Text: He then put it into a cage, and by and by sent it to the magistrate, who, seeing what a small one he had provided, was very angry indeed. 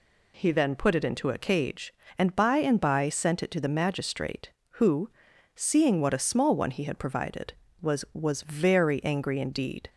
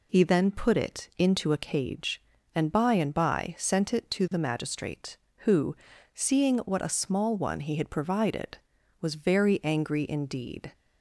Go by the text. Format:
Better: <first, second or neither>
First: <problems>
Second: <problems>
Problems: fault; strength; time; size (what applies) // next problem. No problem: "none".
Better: second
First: says "was" twice; at 8.1 s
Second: none